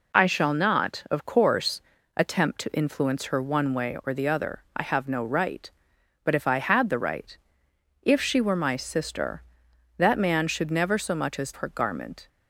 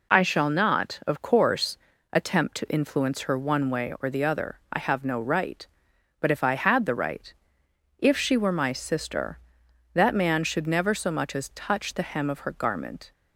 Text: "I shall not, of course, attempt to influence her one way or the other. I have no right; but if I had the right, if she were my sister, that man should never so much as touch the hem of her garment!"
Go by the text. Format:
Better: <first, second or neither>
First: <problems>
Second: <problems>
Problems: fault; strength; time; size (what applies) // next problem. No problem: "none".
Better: second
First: skips "touch the hem of"; at 11.5 s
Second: none